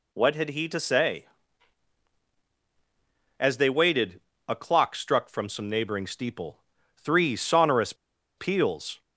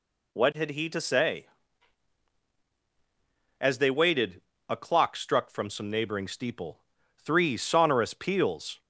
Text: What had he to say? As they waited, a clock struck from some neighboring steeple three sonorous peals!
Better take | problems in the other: second | pauses between "steeple" and "three"; at 6.5 s; 0.44 s long; also in the second // pauses between "sonorous" and "peals"; at 7.9 s; 0.43 s long

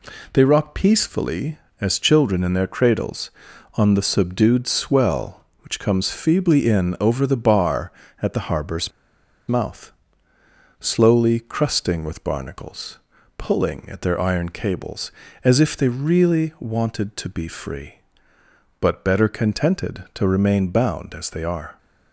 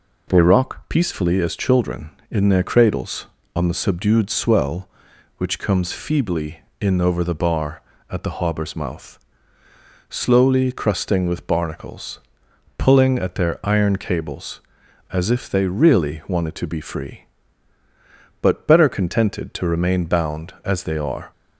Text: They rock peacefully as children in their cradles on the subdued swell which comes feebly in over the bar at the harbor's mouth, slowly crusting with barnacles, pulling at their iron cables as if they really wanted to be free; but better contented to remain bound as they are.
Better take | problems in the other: second | pauses between "harbor's" and "mouth"; noticeable; at 8.9 s; 0.57 s long

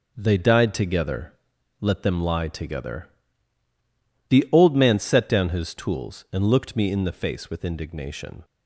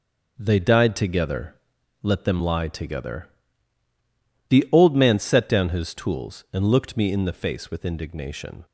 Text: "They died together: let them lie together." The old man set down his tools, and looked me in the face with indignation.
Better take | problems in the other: neither | none

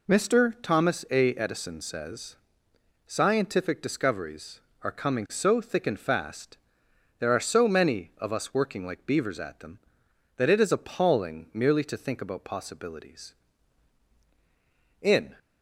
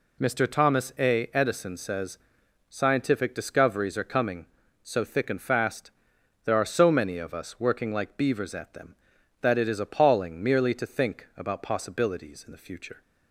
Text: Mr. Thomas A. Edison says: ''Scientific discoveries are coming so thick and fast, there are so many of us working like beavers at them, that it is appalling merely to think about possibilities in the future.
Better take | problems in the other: second | stops before "the future"; at 15.3 s

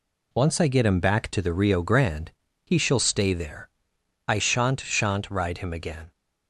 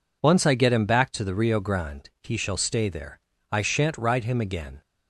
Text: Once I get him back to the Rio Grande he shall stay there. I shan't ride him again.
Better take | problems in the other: second | pauses between "Grande" and "he"; slight; at 2.3 s; 0.32 s long // says "shan't" twice; at 4.7 s

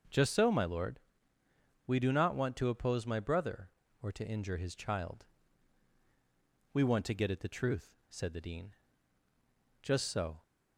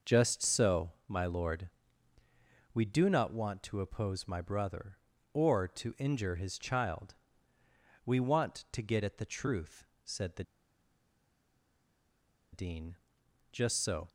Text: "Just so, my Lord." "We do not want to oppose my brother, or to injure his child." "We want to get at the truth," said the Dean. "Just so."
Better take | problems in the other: first | pauses between "the" and "Dean"; strong; at 10.4 s; 2.0 s long

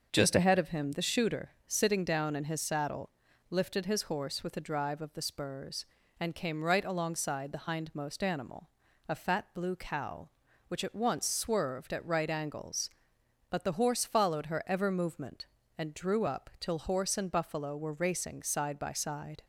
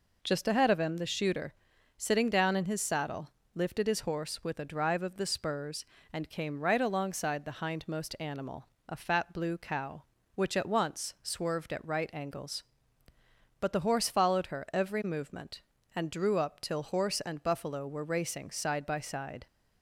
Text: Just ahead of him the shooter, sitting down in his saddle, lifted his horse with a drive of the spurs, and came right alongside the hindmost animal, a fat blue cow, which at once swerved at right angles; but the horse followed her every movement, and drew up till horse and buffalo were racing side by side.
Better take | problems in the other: second | starts louder than the rest; until 1.1 s; 6.5 dB // says "ever" for "every"; at 14.6 s

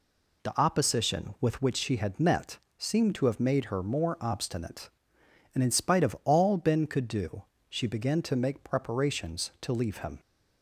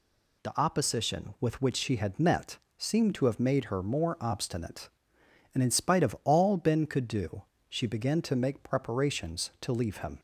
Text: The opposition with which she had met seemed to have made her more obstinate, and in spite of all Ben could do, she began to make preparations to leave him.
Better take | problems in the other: second | starts louder than the rest; slight; until 1.7 s; 2.5 dB // pauses between "met" and "seemed"; slight; at 2.5 s; 0.20 s long; slight in the second

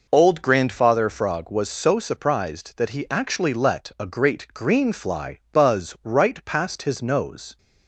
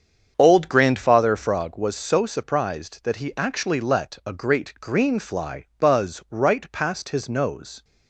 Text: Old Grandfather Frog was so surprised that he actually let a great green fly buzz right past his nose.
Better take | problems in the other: first | starts louder than the rest; strong; until 1.8 s; 7.5 dB

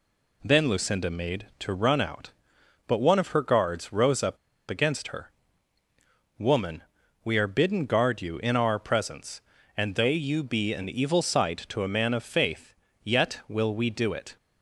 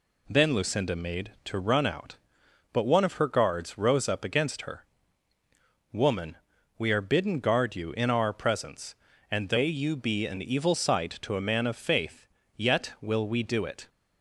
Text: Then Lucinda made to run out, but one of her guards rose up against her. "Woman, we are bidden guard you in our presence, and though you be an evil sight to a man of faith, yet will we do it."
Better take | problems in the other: second | pauses between "up" and "against"; slight; at 4.3 s; 0.33 s long

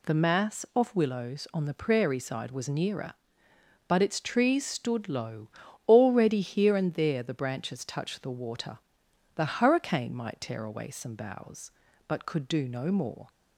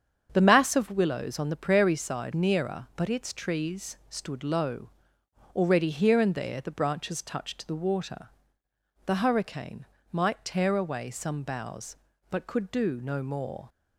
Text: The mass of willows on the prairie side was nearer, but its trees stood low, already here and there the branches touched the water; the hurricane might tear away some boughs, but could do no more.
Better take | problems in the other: first | starts louder than the rest; strong; until 1.3 s; 8 dB // skips "was"; at 2.3 s // pauses between "hurricane" and "might"; slight; at 9.8 s; 0.26 s long

